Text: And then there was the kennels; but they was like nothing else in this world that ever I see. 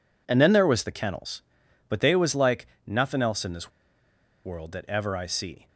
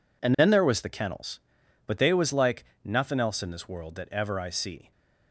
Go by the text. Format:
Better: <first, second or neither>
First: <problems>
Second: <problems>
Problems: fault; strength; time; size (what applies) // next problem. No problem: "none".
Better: second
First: pauses between "like" and "nothing"; slight; at 2.6 s; 0.22 s long // pauses between "this" and "world"; noticeable; at 3.6 s; 0.75 s long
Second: pauses between "like" and "nothing"; slight; at 2.6 s; 0.22 s long